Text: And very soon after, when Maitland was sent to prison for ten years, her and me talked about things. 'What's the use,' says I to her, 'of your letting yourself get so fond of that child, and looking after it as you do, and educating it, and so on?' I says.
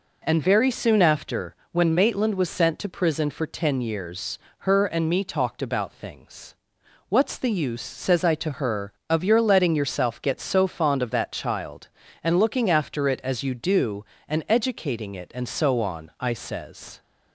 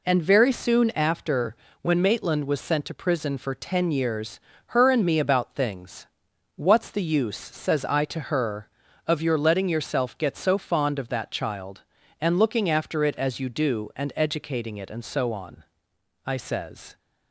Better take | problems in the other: first | skips "talked"; at 5.1 s

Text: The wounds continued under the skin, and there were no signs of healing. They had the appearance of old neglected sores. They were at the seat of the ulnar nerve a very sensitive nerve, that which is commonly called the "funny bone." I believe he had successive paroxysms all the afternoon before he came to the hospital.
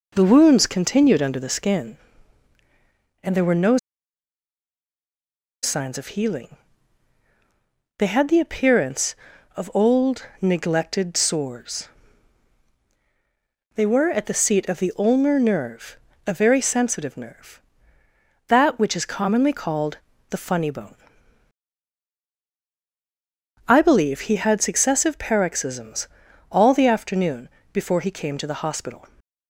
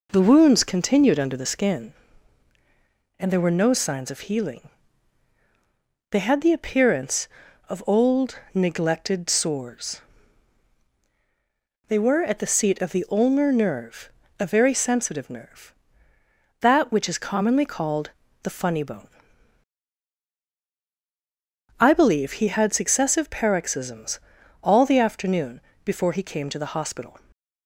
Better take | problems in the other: second | pauses between "no" and "signs"; strong; at 3.7 s; 1.8 s long // pauses between "nerve" and "a"; slight; at 15.9 s; 0.30 s long; slight in the second // pauses between "called" and "the"; slight; at 19.9 s; 0.32 s long; slight in the second // pauses between "paroxysms" and "all"; at 26.0 s; 0.42 s long; also in the second // pauses between "afternoon" and "before"; slight; at 27.4 s; 0.24 s long; slight in the second

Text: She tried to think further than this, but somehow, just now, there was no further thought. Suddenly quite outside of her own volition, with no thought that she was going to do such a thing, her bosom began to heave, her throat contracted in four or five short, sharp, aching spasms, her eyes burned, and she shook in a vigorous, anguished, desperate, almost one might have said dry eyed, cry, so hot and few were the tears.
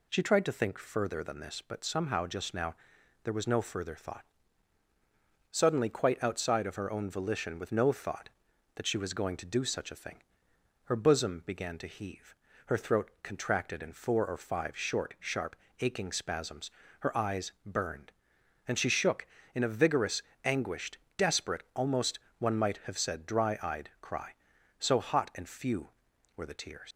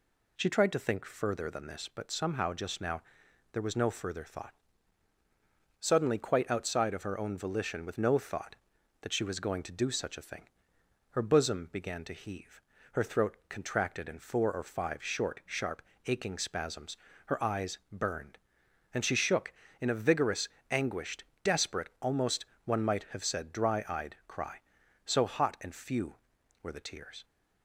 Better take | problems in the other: second | pauses between "almost" and "one"; slight; at 22.1 s; 0.20 s long; slight in the second // leaves "tears" unfinished; at 26.9 s; 70 ms

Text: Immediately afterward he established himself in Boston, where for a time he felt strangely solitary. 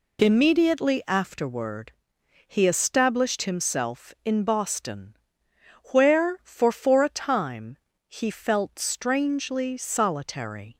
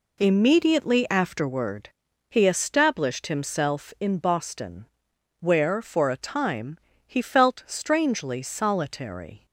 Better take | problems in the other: second | pauses between "afterward" and "he"; noticeable; at 1.9 s; 0.54 s long; also in the second // says "for" twice; at 6.7 s // pauses between "time" and "he"; slight; at 7.7 s; 0.28 s long; slight in the second

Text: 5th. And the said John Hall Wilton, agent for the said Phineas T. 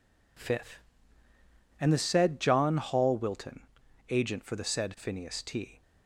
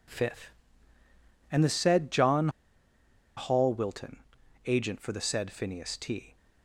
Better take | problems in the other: first | pauses between "John" and "Hall"; noticeable; at 2.4 s; 0.88 s long

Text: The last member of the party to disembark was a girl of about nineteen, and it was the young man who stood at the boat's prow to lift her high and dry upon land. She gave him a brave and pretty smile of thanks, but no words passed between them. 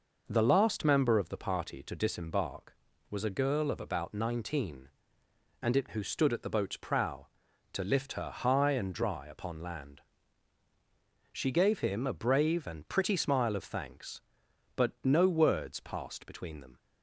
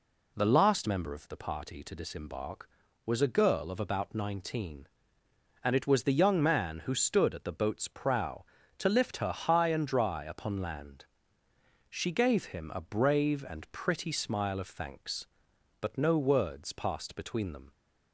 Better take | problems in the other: second | skips "was the young man"; at 5.9 s

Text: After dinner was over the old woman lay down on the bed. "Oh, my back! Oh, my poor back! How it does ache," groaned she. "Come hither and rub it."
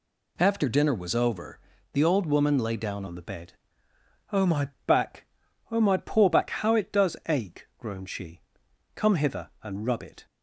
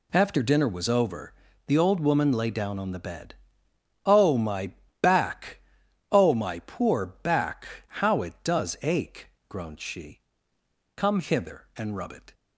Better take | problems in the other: second | pauses between "over" and "the"; slight; at 1.5 s; 0.34 s long; slight in the second // changes voice at "on"; from 3.0 s on; 7.2 s long // pauses between "my" and "back"; slight; at 4.6 s; 0.18 s long; slight in the second

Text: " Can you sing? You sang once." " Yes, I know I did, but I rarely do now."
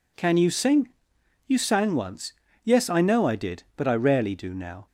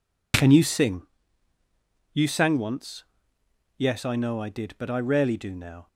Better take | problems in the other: neither | none

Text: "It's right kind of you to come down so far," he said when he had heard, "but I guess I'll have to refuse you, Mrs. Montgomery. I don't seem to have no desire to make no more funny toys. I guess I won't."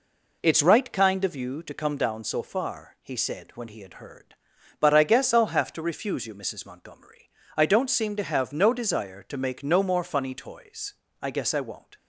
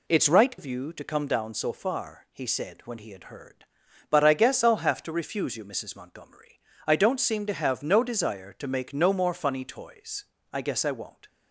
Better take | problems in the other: first | skips "kind"; at 0.5 s

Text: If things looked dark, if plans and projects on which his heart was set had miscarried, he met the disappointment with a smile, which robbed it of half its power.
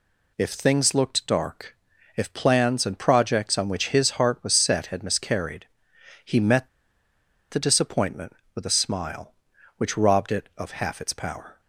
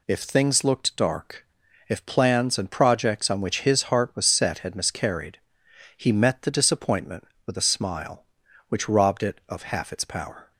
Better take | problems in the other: second | pauses between "met" and "the"; noticeable; at 6.6 s; 0.83 s long

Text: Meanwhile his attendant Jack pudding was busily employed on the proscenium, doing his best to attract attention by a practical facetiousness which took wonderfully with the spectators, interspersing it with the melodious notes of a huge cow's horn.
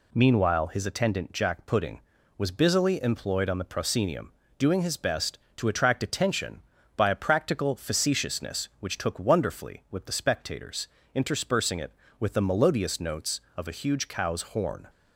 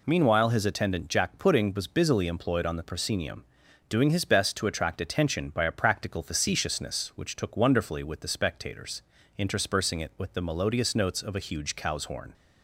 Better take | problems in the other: neither | none

